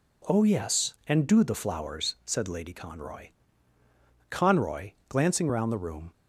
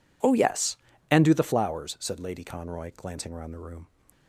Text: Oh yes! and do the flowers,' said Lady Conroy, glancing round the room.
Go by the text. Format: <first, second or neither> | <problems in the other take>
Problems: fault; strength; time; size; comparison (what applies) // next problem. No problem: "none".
second | says "Conroy" twice; at 4.2 s